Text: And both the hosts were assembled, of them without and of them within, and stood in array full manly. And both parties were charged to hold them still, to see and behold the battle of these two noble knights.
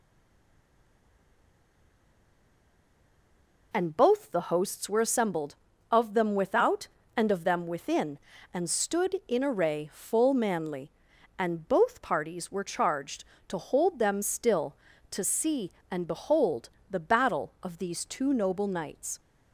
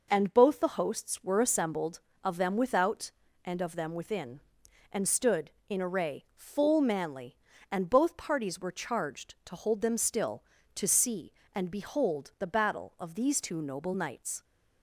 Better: second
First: stays silent before the first word; strong; until 3.7 s; 3.7 s long // pauses between "behold" and "the"; slight; at 16.7 s; 0.20 s long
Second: none

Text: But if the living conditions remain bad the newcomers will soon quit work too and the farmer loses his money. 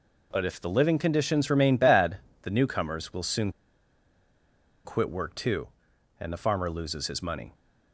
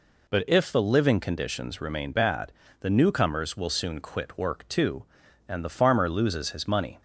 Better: second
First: pauses between "bad" and "the"; slight; at 2.1 s; 0.26 s long // pauses between "soon" and "quit"; strong; at 3.5 s; 1.3 s long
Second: pauses between "bad" and "the"; slight; at 2.5 s; 0.30 s long

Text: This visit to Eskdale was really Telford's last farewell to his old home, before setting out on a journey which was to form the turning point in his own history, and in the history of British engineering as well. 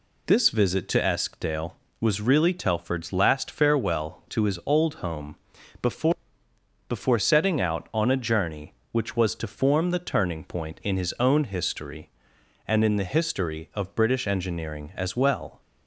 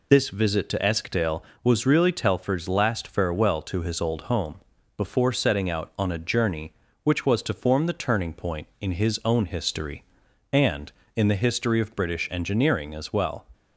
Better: second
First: says "before" twice; at 6.8 s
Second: none

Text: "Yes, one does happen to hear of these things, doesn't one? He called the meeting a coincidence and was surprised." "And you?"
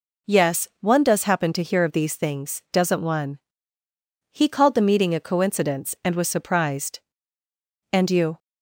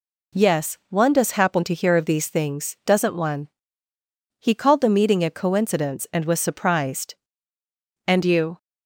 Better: neither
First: none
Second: none

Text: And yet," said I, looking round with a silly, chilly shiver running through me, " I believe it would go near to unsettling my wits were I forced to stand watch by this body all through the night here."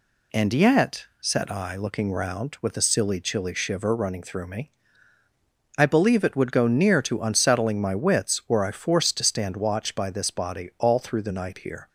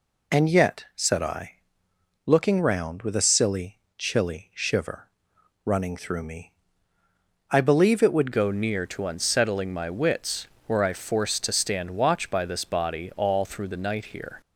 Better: first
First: none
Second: pauses between "shiver" and "running"; noticeable; at 5.0 s; 0.56 s long // changes voice at "go"; from 8.3 s on; 6.1 s long

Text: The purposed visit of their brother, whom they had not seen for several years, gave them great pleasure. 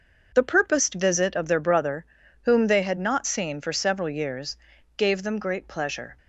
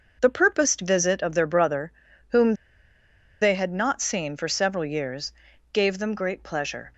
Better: first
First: starts louder than the rest; noticeable; until 1.3 s; 6 dB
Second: starts louder than the rest; noticeable; until 1.2 s; 6 dB // pauses between "whom" and "they"; noticeable; at 2.5 s; 0.88 s long

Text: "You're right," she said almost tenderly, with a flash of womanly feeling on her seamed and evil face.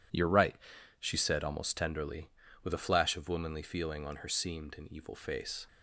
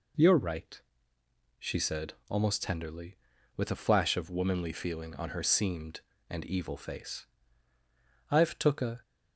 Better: first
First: none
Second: pauses between "said" and "almost"; slight; at 2.1 s; 0.16 s long // goes on to say "I've took a"; noticeable; from 8.3 s on; 0.70 s long

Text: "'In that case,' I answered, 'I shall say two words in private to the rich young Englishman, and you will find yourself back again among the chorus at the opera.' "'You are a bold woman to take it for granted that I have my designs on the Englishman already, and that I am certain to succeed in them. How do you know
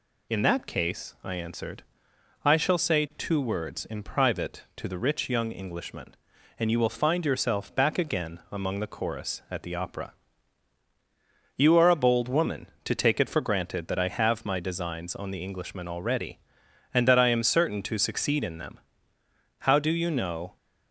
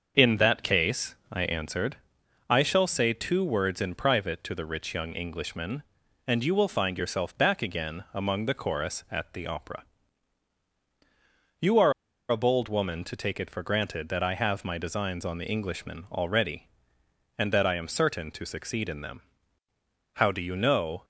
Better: first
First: none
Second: starts louder than the rest; until 1.3 s; 6.5 dB // pauses between "are" and "a"; at 11.9 s; 0.37 s long

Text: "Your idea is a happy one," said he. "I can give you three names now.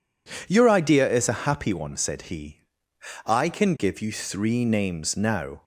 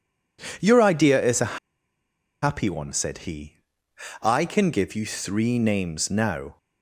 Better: first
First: none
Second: pauses between "a" and "happy"; noticeable; at 1.5 s; 0.84 s long

